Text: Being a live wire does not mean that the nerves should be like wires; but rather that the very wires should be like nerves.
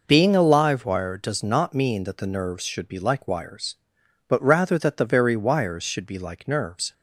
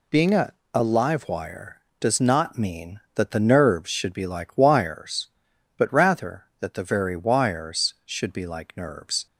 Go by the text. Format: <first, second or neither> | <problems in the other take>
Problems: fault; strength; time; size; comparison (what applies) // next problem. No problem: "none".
first | says "a" twice; at 0.7 s